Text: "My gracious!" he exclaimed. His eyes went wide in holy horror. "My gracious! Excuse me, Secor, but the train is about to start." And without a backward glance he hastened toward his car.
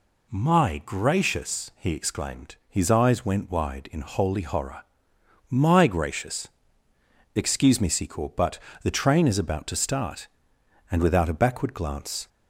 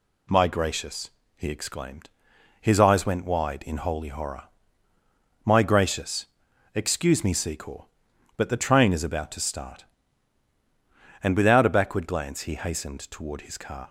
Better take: second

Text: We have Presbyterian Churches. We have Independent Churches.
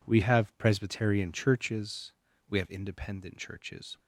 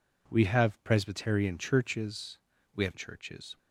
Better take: first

